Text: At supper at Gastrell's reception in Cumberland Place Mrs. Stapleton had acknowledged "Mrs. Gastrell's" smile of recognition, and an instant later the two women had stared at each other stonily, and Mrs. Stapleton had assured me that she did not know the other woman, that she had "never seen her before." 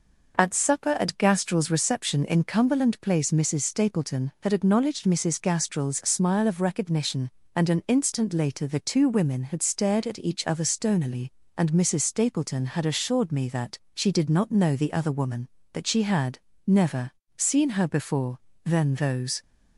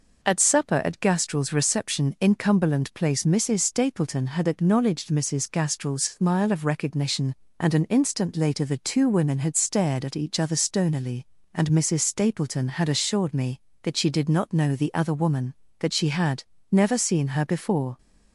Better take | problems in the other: second | pauses between "that" and "she"; slight; at 13.7 s; 0.16 s long // pauses between "had" and "never"; slight; at 16.3 s; 0.28 s long; slight in the second // pauses between "never" and "seen"; slight; at 17.1 s; 0.26 s long // goes on to say "Then those"; noticeable; from 18.6 s on; 0.76 s long

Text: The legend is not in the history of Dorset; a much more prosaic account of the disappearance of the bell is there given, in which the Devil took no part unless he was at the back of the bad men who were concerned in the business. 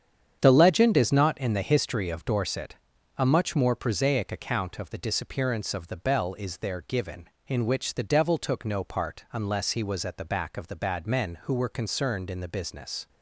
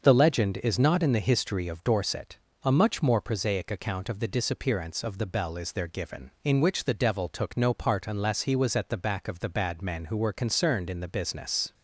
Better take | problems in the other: second | gets quieter; strong; throughout; 9 dB // starts louder than the rest; strong; until 1.4 s; 8 dB; also in the second

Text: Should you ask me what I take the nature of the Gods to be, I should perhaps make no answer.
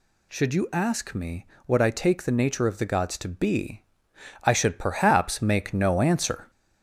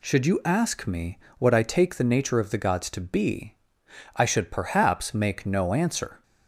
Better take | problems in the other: second | gets louder; slight; throughout; 2.5 dB // pauses between "me" and "what"; slight; at 1.4 s; 0.22 s long; slight in the second

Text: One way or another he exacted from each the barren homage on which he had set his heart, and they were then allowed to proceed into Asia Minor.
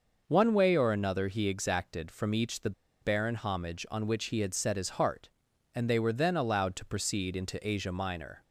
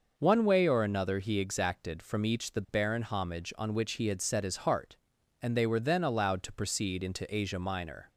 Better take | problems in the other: second | pauses between "the" and "barren"; slight; at 2.7 s; 0.30 s long

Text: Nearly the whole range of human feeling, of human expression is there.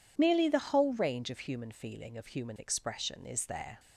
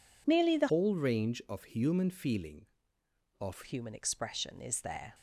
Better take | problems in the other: first | changes voice from "whole" to "of"; from 0.6 to 3.6 s; 3.0 s long

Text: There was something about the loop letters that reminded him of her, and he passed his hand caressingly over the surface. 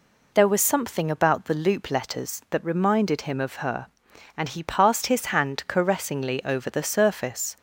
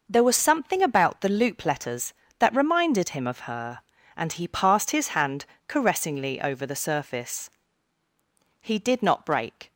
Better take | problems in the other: first | pauses between "hand" and "caressingly"; slight; at 5.4 s; 0.22 s long // goes on to say "He did not break"; noticeable; from 8.6 s on; 1.1 s long

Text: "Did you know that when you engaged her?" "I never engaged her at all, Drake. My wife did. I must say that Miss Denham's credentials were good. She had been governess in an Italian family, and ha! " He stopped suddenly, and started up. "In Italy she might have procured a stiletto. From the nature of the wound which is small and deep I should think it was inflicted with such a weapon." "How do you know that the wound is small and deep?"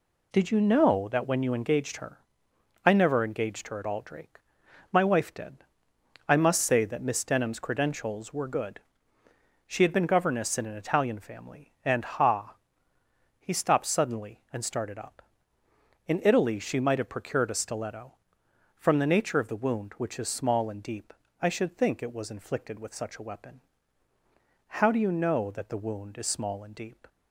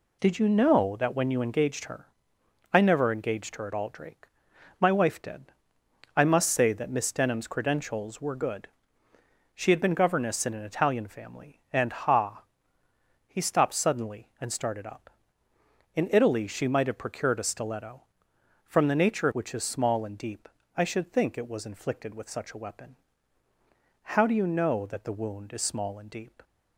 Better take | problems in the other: first | skips "of the wound"; at 19.3 s // pauses between "deep" and "I"; slight; at 20.4 s; 0.30 s long; slight in the first

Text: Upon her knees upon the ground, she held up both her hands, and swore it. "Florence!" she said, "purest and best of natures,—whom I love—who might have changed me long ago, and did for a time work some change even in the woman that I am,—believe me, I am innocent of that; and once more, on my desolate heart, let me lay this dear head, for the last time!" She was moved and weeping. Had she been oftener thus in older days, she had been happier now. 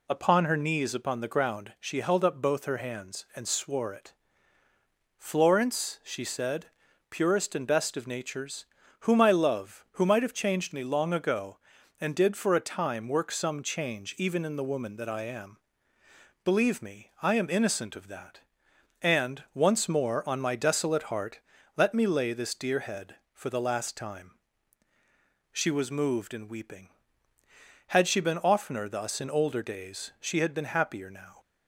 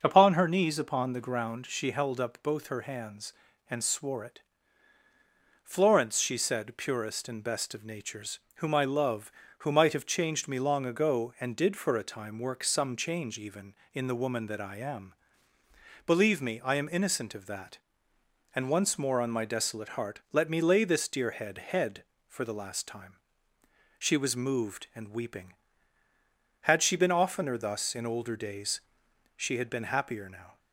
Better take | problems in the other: first | starts louder than the rest; until 1.0 s; 6.5 dB // says "head" twice; at 21.5 s

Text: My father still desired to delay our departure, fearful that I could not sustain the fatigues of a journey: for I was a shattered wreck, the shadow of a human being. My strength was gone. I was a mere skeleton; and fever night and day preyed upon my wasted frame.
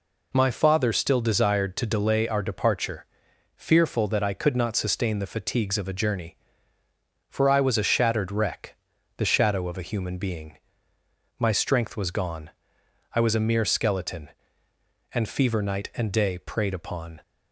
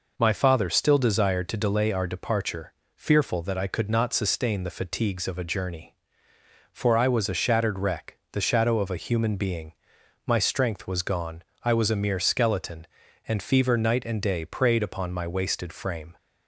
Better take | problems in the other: second | stops before "my wasted frame"; at 17.2 s

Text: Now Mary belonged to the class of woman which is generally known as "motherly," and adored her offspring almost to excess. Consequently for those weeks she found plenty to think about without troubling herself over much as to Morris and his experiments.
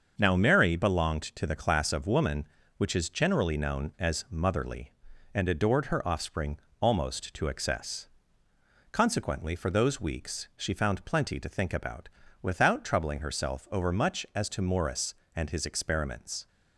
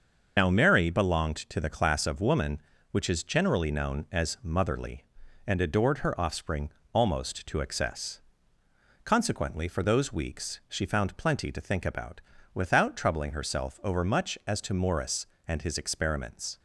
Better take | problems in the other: first | loses the start of "Now"; at 0.3 s; 50 ms // starts louder than the rest; until 1.3 s; 6.5 dB; also in the first // pauses between "offspring" and "almost"; slight; at 6.6 s; 0.24 s long; slight in the first // pauses between "about" and "without"; slight; at 12.2 s; 0.32 s long; slight in the first

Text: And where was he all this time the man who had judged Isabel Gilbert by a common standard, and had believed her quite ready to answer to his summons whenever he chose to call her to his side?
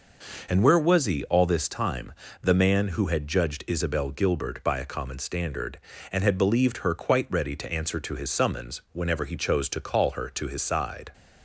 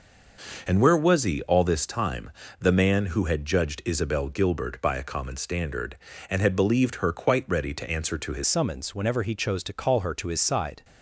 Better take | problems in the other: first | pauses between "time" and "the"; slight; at 2.3 s; 0.28 s long; slight in the first // changes voice at "summons"; from 8.4 s on; 2.4 s long

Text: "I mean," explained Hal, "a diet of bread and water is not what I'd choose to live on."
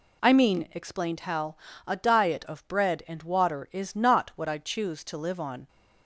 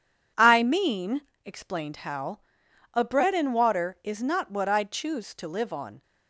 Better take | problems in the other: first | skips "diet of"; at 3.0 s

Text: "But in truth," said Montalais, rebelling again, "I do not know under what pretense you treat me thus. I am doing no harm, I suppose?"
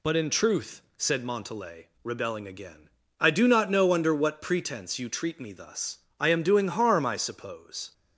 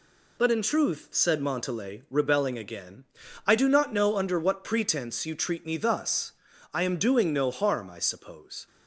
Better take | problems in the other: second | skips "no"; at 6.6 s

